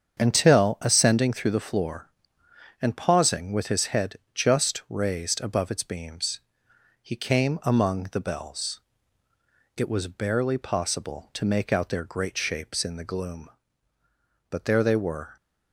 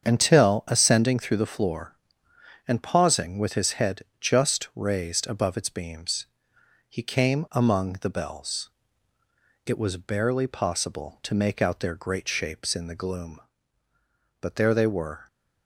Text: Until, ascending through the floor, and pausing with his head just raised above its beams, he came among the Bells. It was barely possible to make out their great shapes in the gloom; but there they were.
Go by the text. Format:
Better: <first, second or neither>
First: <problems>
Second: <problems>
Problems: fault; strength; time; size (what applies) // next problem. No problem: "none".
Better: neither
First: starts louder than the rest; strong; until 1.2 s; 7.5 dB // pauses between "head" and "just"; slight; at 4.1 s; 0.18 s long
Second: starts louder than the rest; strong; until 1.0 s; 7.5 dB // pauses between "head" and "just"; slight; at 4.0 s; 0.18 s long